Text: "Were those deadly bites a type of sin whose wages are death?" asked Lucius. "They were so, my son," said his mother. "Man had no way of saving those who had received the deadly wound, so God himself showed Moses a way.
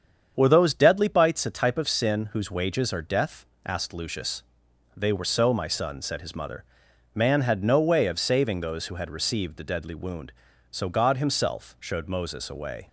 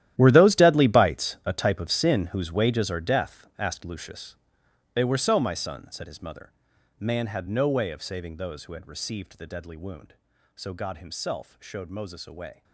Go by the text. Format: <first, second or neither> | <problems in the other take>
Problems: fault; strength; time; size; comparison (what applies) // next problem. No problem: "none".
first | gets quieter; strong; throughout; 16 dB // starts louder than the rest; strong; until 1.1 s; 12.5 dB; strong in the first